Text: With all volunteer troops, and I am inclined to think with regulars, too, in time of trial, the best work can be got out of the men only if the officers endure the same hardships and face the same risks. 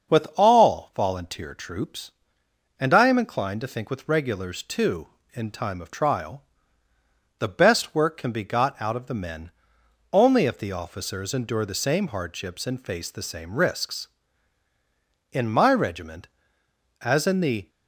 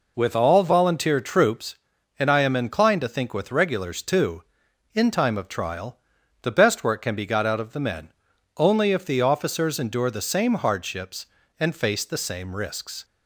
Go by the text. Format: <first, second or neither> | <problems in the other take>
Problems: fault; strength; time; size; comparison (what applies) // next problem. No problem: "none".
second | starts louder than the rest; until 1.2 s; 6.5 dB // pauses between "men" and "only"; noticeable; at 9.5 s; 0.60 s long; noticeable in the second // goes on to say "In my regiment as in the"; strong; from 15.3 s on; 2.3 s long